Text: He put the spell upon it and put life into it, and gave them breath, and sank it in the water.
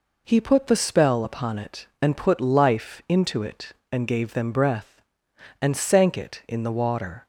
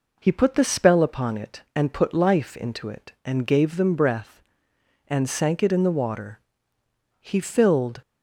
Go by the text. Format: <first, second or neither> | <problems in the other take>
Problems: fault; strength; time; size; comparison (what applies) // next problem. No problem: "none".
first | goes on to say "He filled"; noticeable; from 7.2 s on; 0.80 s long